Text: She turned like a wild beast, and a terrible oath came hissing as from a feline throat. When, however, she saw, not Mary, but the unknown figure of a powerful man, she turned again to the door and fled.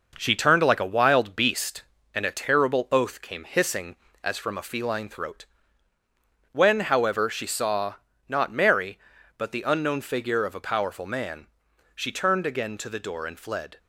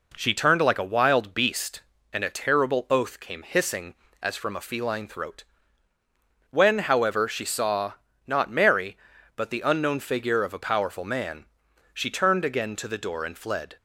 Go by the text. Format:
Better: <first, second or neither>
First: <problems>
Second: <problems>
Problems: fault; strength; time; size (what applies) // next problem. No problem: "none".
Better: second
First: gets quieter; noticeable; throughout; 5.5 dB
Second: none